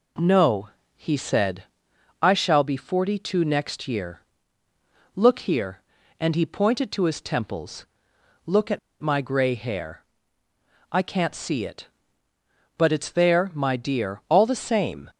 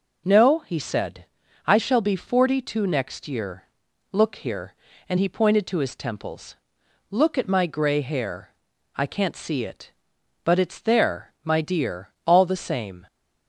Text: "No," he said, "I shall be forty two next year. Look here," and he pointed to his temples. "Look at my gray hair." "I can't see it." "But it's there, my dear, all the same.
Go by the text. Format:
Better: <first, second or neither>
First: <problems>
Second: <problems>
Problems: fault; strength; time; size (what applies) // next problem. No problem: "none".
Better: second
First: pauses between "at" and "my"; slight; at 8.7 s; 0.22 s long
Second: none